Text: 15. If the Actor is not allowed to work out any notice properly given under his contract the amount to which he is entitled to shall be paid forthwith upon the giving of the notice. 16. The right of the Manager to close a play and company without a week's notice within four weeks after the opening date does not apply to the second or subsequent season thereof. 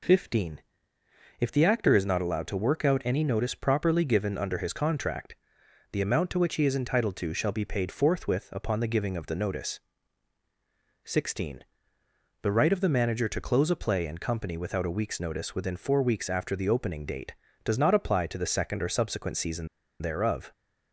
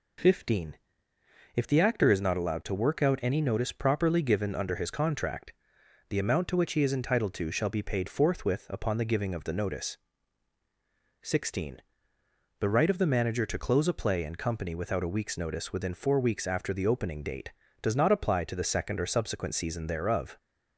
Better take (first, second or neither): second